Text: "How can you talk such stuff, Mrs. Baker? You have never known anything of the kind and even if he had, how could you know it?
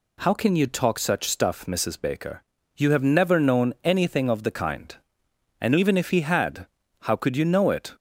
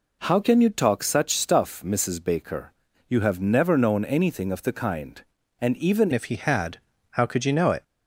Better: first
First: none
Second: changes voice at "if"; from 6.1 s on; 1.7 s long

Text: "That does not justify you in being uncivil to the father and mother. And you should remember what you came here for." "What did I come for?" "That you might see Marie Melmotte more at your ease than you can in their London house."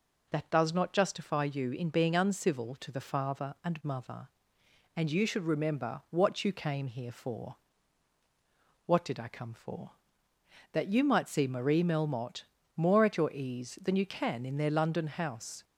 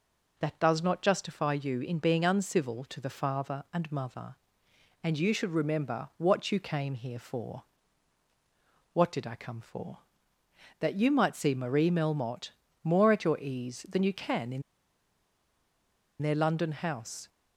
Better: first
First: pauses between "Melmotte" and "more"; slight; at 12.4 s; 0.32 s long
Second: pauses between "Melmotte" and "more"; slight; at 12.5 s; 0.32 s long // pauses between "in" and "their"; strong; at 14.6 s; 1.6 s long

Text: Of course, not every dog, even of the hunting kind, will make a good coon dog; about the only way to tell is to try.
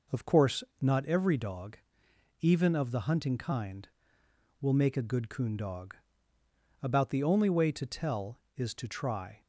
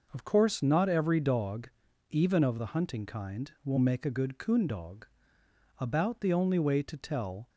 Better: first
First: none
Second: stops before "is to try"; at 7.4 s

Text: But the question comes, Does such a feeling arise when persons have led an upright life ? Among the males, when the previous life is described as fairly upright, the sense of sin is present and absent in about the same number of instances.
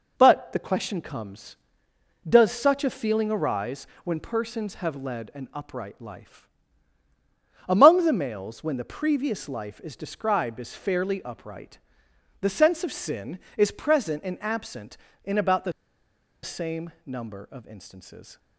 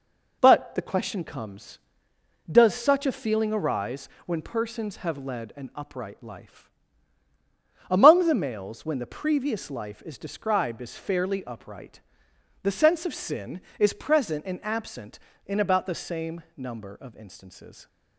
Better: second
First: pauses between "arise" and "when"; slight; at 3.8 s; 0.16 s long // pauses between "the" and "same"; noticeable; at 15.7 s; 0.72 s long // pauses between "same" and "number"; slight; at 16.9 s; 0.16 s long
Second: pauses between "arise" and "when"; slight; at 4.0 s; 0.16 s long // pauses between "same" and "number"; slight; at 16.4 s; 0.16 s long

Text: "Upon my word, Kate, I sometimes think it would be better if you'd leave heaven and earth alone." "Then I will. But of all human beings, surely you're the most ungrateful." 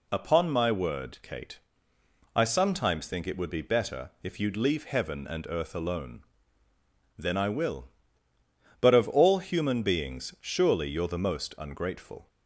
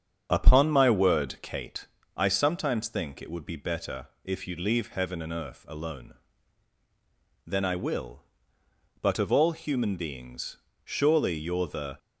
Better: first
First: none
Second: starts louder than the rest; strong; until 1.3 s; 7 dB // pauses between "better" and "if"; slight; at 4.0 s; 0.16 s long // stops before "most ungrateful"; at 11.9 s

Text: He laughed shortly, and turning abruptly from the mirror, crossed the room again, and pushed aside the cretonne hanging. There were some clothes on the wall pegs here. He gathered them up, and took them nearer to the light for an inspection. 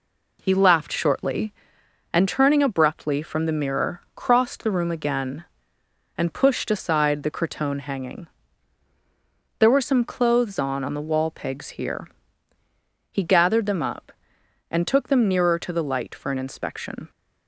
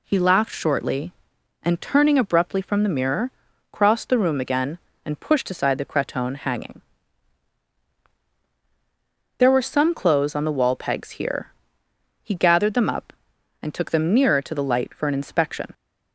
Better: second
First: says "on" twice; at 10.8 s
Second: none

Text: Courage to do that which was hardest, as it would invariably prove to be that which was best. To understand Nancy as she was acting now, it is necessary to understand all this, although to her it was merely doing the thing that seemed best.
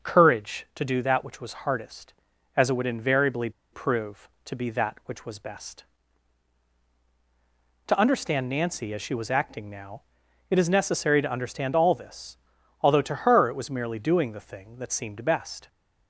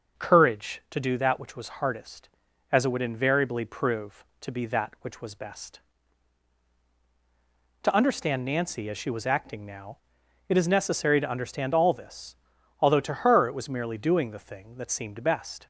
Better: second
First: starts louder than the rest; until 1.1 s; 6 dB // pauses between "invariably" and "prove"; slight; at 3.5 s; 0.22 s long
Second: starts louder than the rest; until 1.2 s; 6 dB

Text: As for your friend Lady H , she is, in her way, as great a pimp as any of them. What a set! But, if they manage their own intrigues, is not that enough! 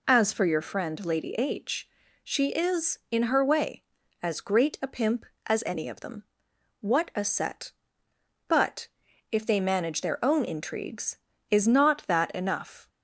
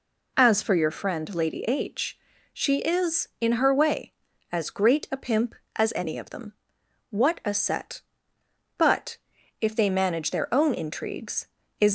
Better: first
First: none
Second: stops before "not that enough"; at 11.8 s

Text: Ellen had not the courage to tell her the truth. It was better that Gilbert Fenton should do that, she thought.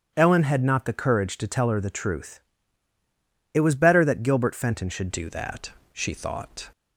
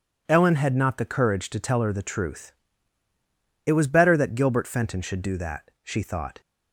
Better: second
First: starts louder than the rest; strong; until 1.1 s; 8 dB // changes voice at "do"; from 5.1 s on; 1.5 s long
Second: none

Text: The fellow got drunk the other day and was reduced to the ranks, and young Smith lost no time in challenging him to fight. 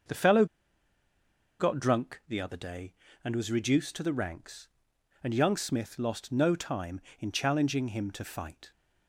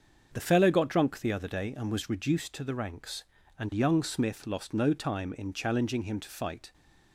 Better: second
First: starts louder than the rest; noticeable; until 2.3 s; 6 dB // pauses between "fellow" and "got"; at 0.4 s; 1.1 s long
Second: starts louder than the rest; until 1.3 s; 6.5 dB

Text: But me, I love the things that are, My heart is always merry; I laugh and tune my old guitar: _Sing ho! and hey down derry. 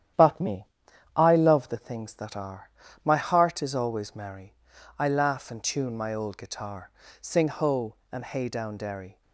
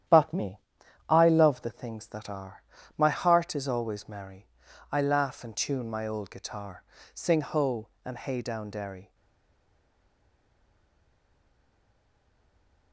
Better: first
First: starts louder than the rest; strong; until 1.6 s; 10.5 dB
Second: starts louder than the rest; strong; until 1.5 s; 10.5 dB // stays silent after the last word; strong; from 9.1 s on; 3.8 s long

